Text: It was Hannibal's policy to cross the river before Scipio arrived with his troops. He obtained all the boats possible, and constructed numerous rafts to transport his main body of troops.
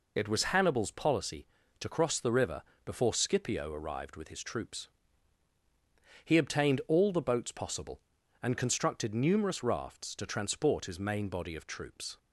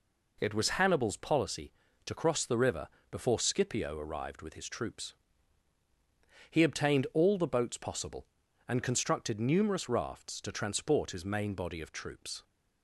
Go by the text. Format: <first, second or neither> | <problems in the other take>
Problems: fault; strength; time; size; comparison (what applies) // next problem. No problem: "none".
second | loses the start of "It"; at 0.1 s; 35 ms // pauses between "river" and "before"; slight; at 2.6 s; 0.24 s long; slight in the second